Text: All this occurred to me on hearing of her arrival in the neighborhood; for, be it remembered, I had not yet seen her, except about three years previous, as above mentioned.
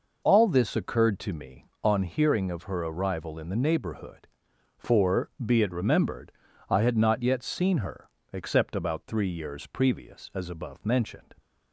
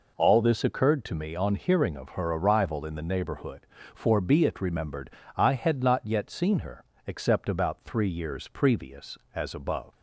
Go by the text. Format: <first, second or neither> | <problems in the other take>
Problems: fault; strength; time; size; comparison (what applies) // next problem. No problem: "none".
first | stops before "mentioned"; at 9.9 s